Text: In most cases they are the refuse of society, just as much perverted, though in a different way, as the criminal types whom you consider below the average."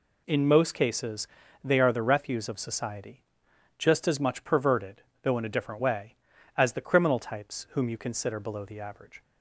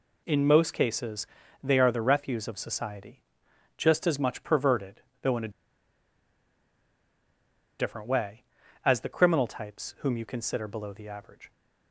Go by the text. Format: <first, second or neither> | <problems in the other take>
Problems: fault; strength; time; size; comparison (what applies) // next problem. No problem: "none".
first | pauses between "cases" and "they"; slight; at 1.2 s; 0.36 s long; slight in the first // pauses between "a" and "different"; strong; at 5.4 s; 2.2 s long